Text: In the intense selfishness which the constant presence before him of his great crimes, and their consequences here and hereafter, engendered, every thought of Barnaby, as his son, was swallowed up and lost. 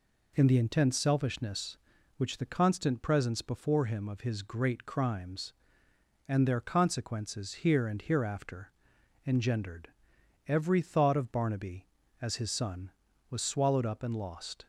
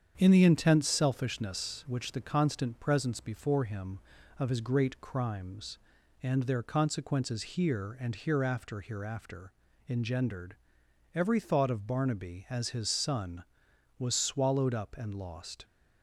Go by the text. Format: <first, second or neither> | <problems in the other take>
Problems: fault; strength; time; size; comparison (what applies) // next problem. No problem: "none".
first | starts louder than the rest; strong; until 1.1 s; 8 dB // says "hereafter" twice; at 8.8 s